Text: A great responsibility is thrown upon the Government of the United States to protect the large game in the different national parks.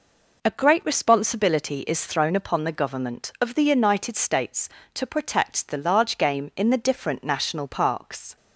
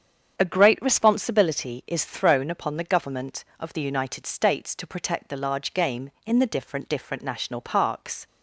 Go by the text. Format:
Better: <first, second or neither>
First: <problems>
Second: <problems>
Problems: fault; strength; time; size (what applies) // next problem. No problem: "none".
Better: first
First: none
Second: starts louder than the rest; strong; until 1.4 s; 8 dB // says "different" twice; at 6.8 s